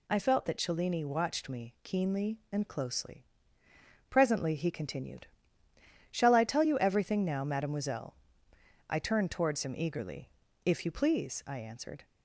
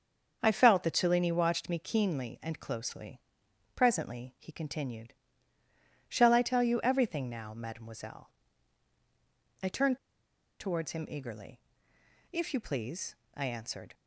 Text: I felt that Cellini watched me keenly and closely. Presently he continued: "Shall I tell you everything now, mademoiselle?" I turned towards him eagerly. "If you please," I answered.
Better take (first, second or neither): first